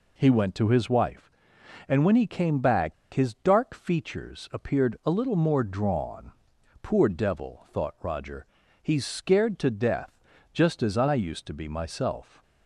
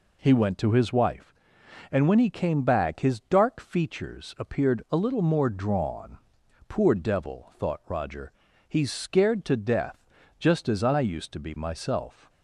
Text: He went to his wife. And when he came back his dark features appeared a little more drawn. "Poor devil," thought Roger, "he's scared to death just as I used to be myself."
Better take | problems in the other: second | pauses between "back" and "his"; slight; at 2.9 s; 0.19 s long // pauses between "death" and "just"; slight; at 10.1 s; 0.32 s long; slight in the second

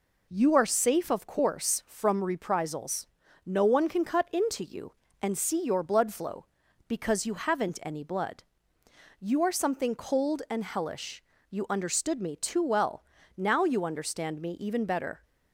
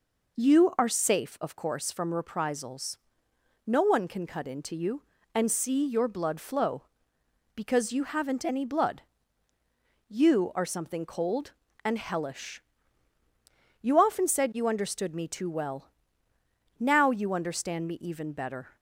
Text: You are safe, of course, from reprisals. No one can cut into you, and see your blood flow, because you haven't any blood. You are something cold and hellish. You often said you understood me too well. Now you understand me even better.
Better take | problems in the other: second | skips "You often said"; at 11.3 s

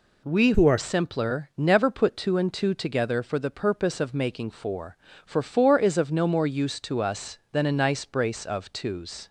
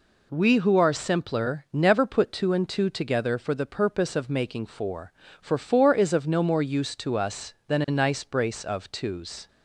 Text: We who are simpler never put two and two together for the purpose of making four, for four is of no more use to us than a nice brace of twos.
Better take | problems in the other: second | changes voice from "who" to "are"; from 0.5 to 0.7 s; 0.2 s long

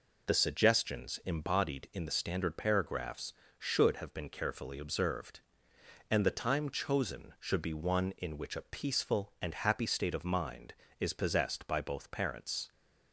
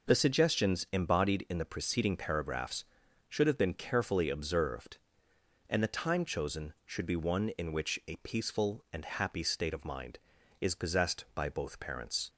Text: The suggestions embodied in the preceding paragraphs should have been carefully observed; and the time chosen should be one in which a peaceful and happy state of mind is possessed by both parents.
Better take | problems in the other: second | says "standard" for "preceding"; at 2.1 s

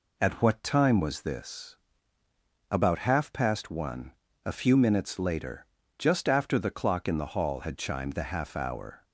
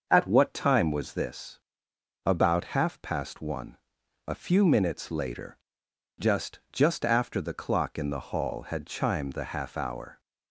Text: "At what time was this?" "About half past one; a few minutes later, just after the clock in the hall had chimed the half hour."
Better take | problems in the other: first | starts louder than the rest; until 1.1 s; 6 dB // says "just" twice; at 6.7 s

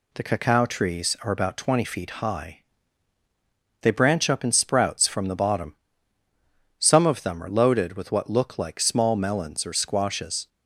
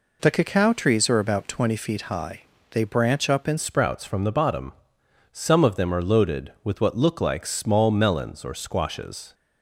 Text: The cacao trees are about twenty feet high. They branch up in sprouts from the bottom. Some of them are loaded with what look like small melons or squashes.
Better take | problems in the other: first | changes voice at "sprouts"; from 3.5 s on; 5.8 s long

